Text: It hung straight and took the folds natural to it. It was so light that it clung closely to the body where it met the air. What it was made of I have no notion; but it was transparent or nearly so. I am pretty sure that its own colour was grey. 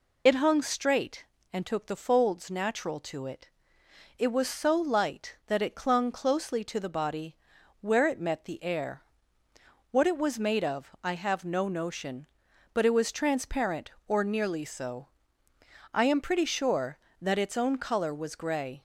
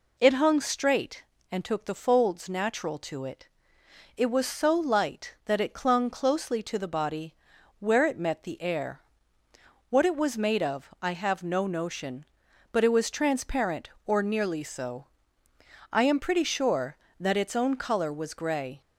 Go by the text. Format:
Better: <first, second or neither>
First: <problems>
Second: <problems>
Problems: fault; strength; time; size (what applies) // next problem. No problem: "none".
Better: second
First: loses the start of "It"; at 0.2 s; 55 ms // pauses between "body" and "where"; noticeable; at 7.3 s; 0.46 s long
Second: pauses between "body" and "where"; noticeable; at 7.3 s; 0.46 s long